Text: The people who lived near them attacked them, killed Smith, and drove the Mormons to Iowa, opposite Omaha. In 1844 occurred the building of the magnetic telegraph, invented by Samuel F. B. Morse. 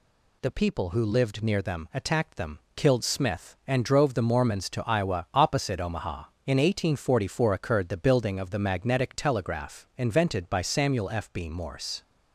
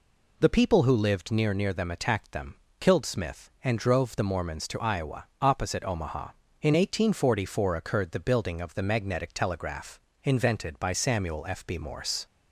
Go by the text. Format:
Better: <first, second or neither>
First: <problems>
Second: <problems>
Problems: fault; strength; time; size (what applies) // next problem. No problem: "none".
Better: first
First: none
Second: says "near" twice; at 1.5 s